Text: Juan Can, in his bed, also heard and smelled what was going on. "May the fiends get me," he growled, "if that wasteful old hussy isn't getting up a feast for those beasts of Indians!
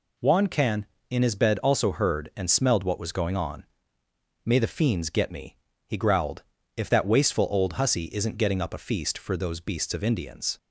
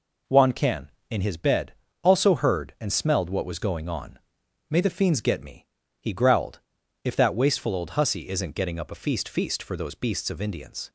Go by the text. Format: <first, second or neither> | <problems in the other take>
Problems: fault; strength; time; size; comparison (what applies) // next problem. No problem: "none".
first | says "feast" twice; at 9.2 s